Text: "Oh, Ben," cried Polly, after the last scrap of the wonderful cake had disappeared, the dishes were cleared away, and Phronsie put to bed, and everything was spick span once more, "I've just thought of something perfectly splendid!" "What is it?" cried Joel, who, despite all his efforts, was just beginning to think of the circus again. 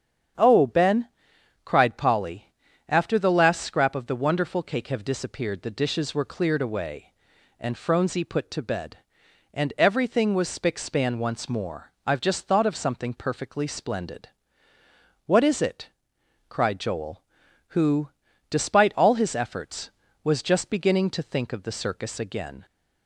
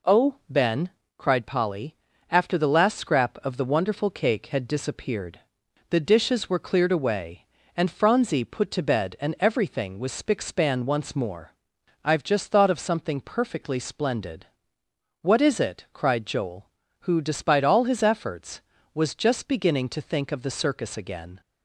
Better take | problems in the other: second | starts louder than the rest; strong; until 1.9 s; 8.5 dB // says "have" for "had"; at 4.8 s

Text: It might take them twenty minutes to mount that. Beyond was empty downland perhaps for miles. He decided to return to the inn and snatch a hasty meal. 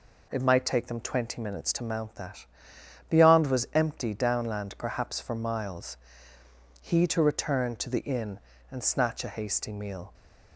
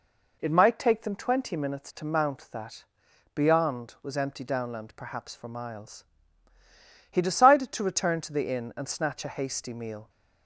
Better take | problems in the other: second | skips "decided"; at 7.0 s

